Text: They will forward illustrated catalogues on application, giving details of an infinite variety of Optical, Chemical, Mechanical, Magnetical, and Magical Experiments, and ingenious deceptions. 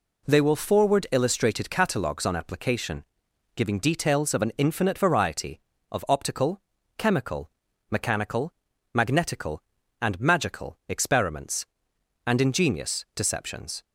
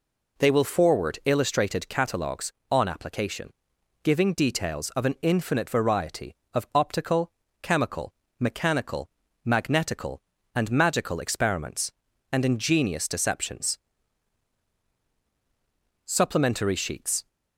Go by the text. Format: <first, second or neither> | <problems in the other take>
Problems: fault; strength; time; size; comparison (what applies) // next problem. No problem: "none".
first | goes on to say "Supplementary sheets"; noticeable; from 16.0 s on; 1.2 s long